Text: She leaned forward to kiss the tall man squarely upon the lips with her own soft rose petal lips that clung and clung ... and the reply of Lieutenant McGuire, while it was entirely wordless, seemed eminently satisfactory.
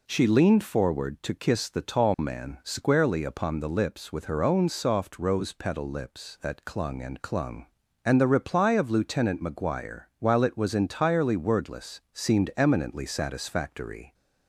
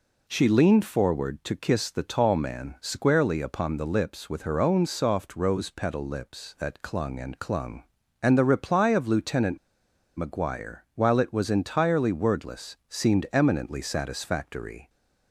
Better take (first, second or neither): first